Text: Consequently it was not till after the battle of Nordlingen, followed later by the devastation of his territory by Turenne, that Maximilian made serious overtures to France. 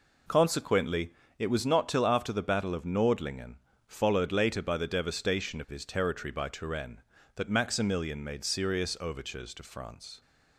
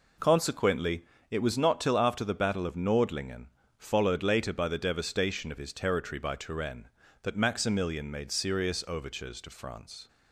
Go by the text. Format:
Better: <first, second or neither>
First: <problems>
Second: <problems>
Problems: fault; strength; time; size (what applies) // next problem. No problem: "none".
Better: neither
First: pauses between "Consequently" and "it"; slight; at 1.1 s; 0.26 s long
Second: pauses between "Consequently" and "it"; slight; at 1.0 s; 0.26 s long